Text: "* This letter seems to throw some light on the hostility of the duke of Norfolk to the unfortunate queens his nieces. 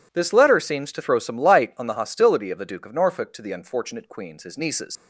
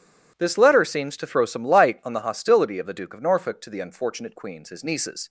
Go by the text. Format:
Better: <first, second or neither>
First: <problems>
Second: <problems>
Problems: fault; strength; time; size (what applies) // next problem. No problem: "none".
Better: second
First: leaves "nieces" unfinished; at 4.9 s; 70 ms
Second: none